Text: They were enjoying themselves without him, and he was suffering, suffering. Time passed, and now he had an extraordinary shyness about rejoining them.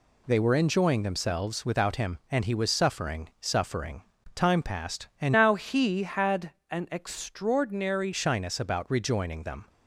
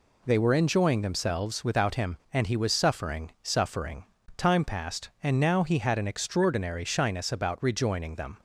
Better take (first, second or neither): second